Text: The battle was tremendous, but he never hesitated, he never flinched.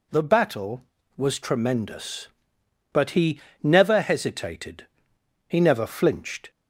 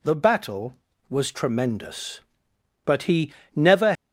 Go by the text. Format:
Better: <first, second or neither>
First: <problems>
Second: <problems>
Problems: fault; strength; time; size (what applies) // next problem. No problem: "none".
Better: first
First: pauses between "he" and "never"; slight; at 3.3 s; 0.22 s long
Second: pauses between "he" and "never"; slight; at 3.3 s; 0.22 s long // stops before "hesitated he never flinched"; at 3.9 s